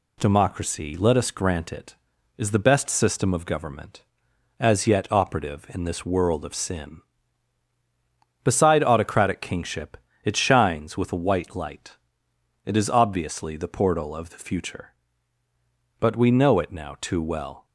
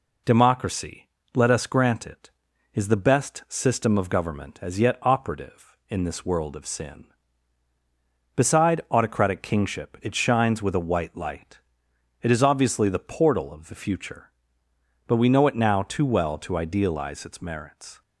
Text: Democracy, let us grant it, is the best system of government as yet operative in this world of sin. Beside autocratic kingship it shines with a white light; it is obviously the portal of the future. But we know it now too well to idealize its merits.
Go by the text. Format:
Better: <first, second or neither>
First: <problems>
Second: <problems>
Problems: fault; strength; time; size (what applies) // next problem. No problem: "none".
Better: second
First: pauses between "kingship" and "it"; slight; at 9.9 s; 0.30 s long // stops before "to idealize its merits"; at 17.6 s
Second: none